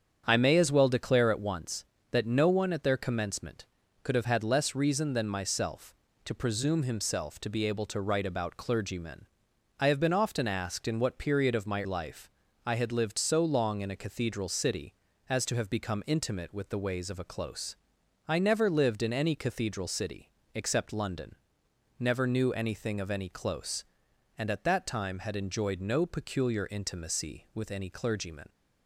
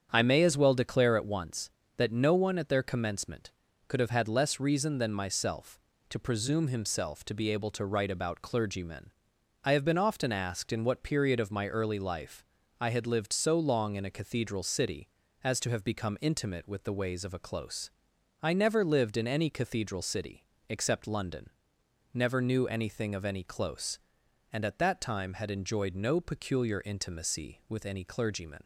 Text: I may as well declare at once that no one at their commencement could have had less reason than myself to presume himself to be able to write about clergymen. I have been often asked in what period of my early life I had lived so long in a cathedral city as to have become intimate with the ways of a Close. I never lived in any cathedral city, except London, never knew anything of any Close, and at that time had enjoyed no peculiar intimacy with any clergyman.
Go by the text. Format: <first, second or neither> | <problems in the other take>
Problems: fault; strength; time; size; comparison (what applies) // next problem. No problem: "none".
second | starts louder than the rest; strong; until 1.2 s; 8 dB; strong in the second // skips "early"; at 11.8 s // pauses between "life" and "I"; at 12.2 s; 0.38 s long; also in the second